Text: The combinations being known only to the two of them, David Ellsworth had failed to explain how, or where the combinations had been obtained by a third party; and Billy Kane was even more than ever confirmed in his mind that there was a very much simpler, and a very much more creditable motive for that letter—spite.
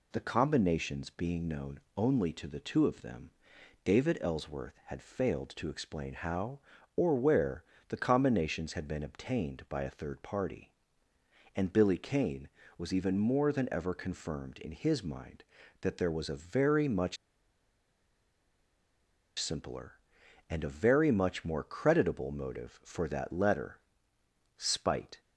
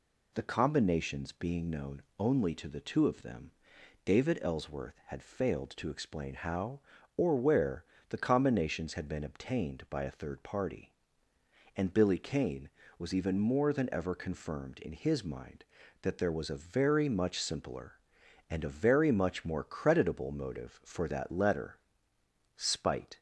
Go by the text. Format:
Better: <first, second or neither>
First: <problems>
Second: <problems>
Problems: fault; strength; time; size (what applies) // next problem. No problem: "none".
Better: second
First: pauses between "known" and "only"; slight; at 1.7 s; 0.16 s long // pauses between "where" and "the"; slight; at 7.6 s; 0.24 s long // pauses between "much" and "simpler"; strong; at 17.1 s; 2.2 s long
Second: pauses between "known" and "only"; slight; at 2.0 s; 0.16 s long // pauses between "where" and "the"; slight; at 7.8 s; 0.24 s long